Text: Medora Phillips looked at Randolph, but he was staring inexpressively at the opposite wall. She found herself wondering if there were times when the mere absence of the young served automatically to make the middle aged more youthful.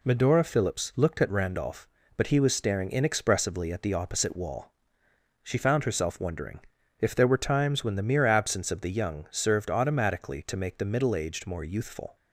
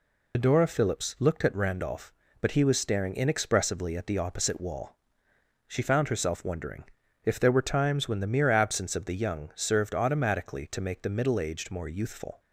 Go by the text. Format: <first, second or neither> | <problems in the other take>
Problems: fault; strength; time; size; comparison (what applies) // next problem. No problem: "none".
first | loses the start of "Medora"; at 0.3 s; 85 ms // pauses between "wondering" and "if"; at 6.8 s; 0.40 s long; also in the first